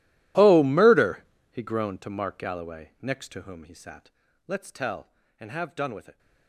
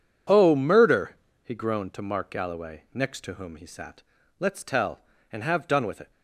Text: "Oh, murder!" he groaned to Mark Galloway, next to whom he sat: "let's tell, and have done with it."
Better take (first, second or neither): second